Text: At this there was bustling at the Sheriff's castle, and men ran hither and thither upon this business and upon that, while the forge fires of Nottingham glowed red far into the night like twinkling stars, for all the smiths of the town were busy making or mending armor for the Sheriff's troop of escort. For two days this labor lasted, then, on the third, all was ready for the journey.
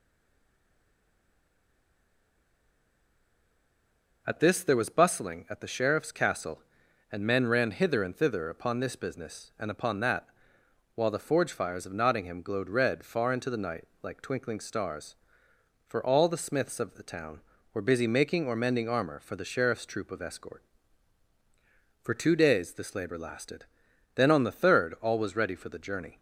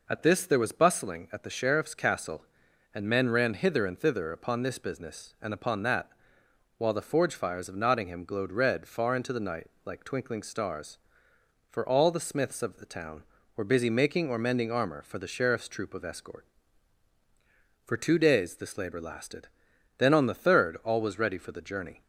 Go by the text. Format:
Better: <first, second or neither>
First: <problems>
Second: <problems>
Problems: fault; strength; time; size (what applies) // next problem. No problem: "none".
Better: second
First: stays silent before the first word; strong; until 4.2 s; 4.2 s long // pauses between "night" and "like"; slight; at 13.8 s; 0.16 s long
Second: pauses between "night" and "like"; slight; at 9.6 s; 0.16 s long